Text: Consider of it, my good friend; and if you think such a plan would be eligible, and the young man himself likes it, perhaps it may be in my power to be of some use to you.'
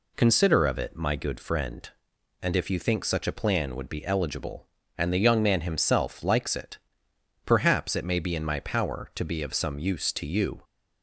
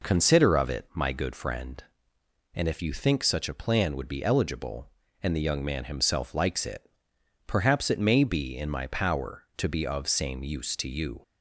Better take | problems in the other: first | says "same" for "some"; at 10.0 s

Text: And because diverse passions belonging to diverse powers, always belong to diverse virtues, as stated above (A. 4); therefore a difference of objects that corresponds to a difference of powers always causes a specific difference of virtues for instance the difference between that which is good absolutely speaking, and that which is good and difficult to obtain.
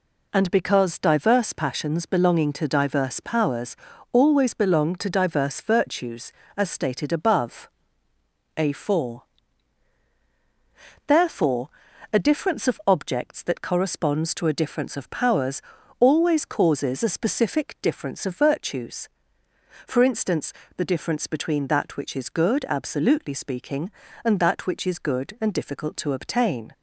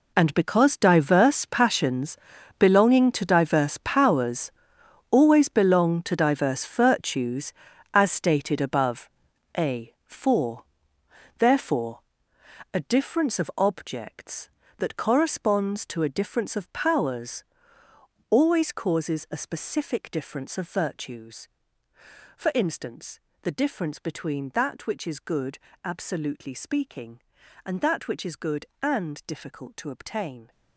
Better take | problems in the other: first | gets quieter; strong; throughout; 15 dB // pauses between "passions" and "belonging"; at 2.1 s; 0.42 s long // pauses between "therefore" and "a"; noticeable; at 12.0 s; 0.72 s long; also in the first // pauses between "powers" and "always"; noticeable; at 17.4 s; 0.88 s long; slight in the first // pauses between "instance" and "the"; slight; at 23.1 s; 0.24 s long; slight in the first // pauses between "good" and "absolutely"; slight; at 25.5 s; 0.25 s long

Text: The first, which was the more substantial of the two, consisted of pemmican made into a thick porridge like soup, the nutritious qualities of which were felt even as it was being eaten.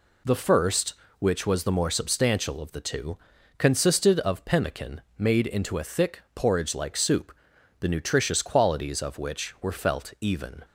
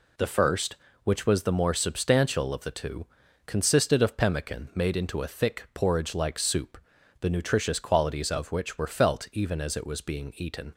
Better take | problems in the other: second | pauses between "pemmican" and "made"; slight; at 5.0 s; 0.16 s long // stops before "as it was being eaten"; at 10.6 s

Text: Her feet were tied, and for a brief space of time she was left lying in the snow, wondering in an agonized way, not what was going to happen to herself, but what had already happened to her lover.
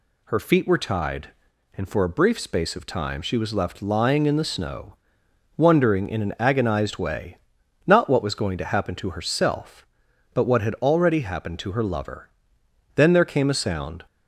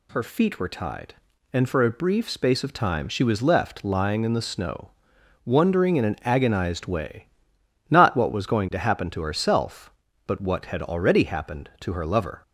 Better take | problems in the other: second | goes on to say "Then there came a sound"; noticeable; from 12.9 s on; 1.1 s long

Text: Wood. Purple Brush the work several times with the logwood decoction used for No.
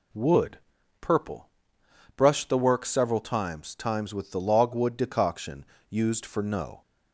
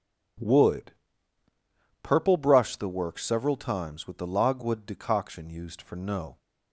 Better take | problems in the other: second | pauses between "Purple" and "Brush"; noticeable; at 1.4 s; 0.70 s long // says "times" twice; at 3.7 s // pauses between "decoction" and "used"; slight; at 5.6 s; 0.26 s long

